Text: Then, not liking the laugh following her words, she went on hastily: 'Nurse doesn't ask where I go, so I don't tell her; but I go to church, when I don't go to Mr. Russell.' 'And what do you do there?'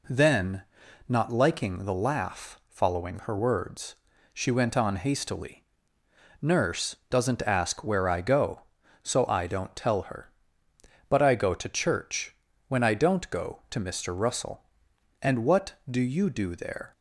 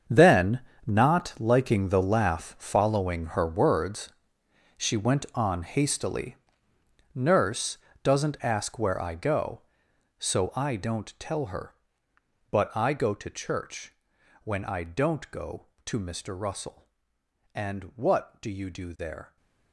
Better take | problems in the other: first | gets quieter; strong; throughout; 13.5 dB // pauses between "Nurse" and "doesn't"; slight; at 7.7 s; 0.26 s long

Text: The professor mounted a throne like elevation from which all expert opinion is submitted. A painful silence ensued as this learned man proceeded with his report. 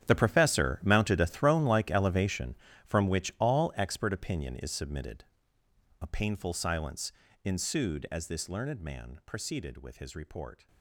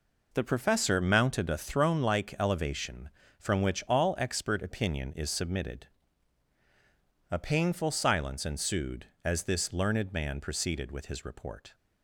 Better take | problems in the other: second | gets quieter; strong; throughout; 16.5 dB // pauses between "silence" and "ensued"; slight; at 7.1 s; 0.30 s long

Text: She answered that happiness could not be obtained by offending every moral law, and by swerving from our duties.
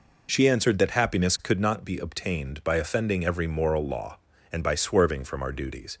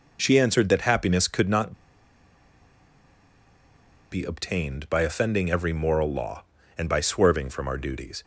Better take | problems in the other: first | pauses between "not" and "be"; strong; at 1.7 s; 2.3 s long

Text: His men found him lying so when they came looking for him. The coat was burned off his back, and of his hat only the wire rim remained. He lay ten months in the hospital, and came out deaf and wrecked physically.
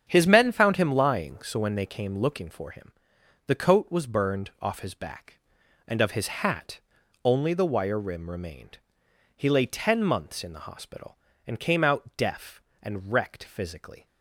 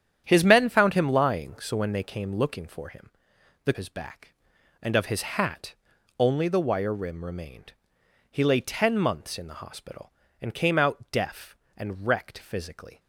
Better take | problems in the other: first | starts louder than the rest; strong; until 1.2 s; 9.5 dB; strong in the first // skips "coat was burned off"; at 3.7 s // pauses between "hat" and "only"; noticeable; at 5.7 s; 0.46 s long; noticeable in the first

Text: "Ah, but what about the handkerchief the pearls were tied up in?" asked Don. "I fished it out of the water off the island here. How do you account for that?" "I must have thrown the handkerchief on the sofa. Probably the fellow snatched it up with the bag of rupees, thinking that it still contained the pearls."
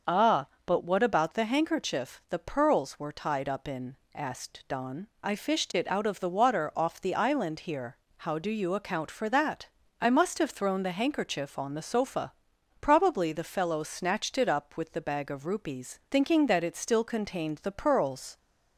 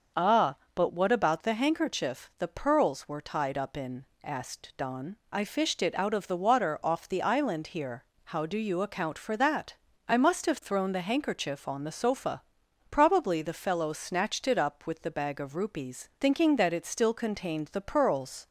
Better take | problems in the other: neither | starts louder than the rest; the same in both

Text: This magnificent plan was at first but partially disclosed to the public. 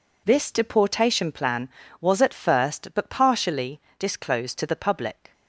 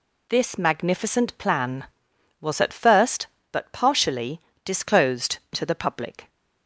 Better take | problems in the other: second | says "deportation" for "magnificent"; at 0.5 s // pauses between "partially" and "disclosed"; slight; at 3.8 s; 0.16 s long; slight in the second

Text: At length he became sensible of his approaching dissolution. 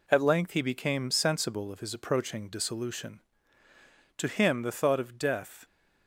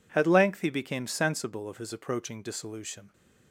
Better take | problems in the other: second | goes on to say "To him the thought of death"; from 4.1 s on; 1.4 s long

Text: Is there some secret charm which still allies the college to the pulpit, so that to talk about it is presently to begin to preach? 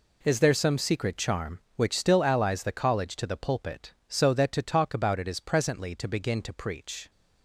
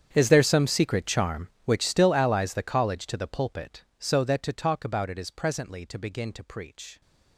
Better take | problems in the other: first | gets quieter; strong; throughout; 21 dB

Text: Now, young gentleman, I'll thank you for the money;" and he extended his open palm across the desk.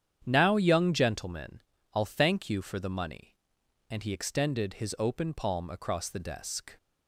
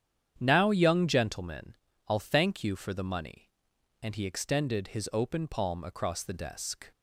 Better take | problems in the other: neither | starts louder than the rest; strong; the same in both

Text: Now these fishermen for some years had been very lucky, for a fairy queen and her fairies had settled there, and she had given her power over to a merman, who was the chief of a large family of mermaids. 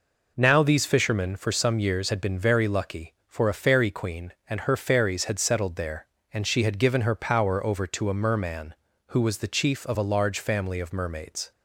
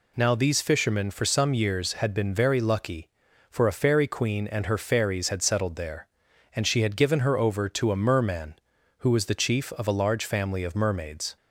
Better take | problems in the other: first | skips "power"; at 7.3 s

